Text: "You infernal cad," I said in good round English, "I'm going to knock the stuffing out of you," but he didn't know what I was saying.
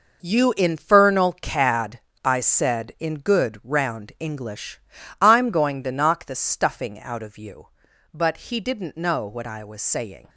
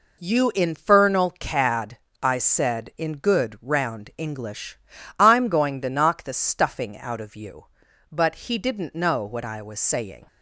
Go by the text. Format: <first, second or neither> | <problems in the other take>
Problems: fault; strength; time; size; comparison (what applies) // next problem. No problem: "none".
second | gets quieter; strong; throughout; 11 dB